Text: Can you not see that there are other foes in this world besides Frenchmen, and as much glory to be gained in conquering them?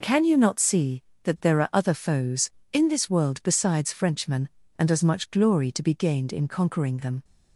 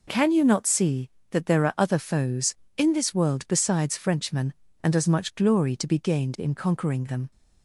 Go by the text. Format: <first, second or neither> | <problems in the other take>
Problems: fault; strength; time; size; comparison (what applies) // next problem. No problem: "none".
neither | none